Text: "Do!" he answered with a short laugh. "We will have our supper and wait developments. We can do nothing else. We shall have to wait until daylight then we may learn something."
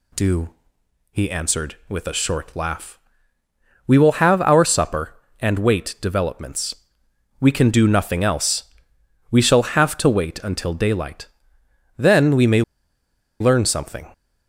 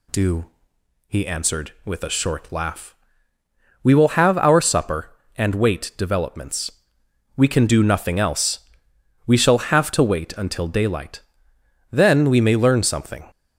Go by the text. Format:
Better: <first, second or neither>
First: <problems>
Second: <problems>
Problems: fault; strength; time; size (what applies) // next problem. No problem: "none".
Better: second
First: pauses between "daylight" and "then"; noticeable; at 11.2 s; 0.72 s long // pauses between "may" and "learn"; noticeable; at 12.6 s; 0.79 s long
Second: pauses between "daylight" and "then"; noticeable; at 11.1 s; 0.72 s long